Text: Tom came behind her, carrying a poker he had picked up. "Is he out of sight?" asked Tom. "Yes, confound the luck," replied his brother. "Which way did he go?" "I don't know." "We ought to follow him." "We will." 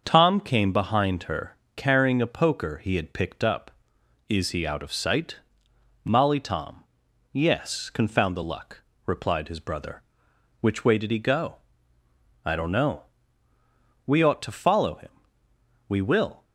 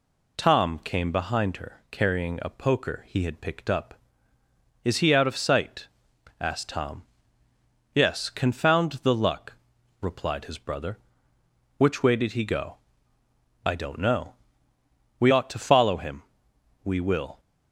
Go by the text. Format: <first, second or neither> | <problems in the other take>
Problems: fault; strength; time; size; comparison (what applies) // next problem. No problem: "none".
second | starts louder than the rest; until 1.0 s; 6.5 dB // says "molly" for "asked"; at 6.0 s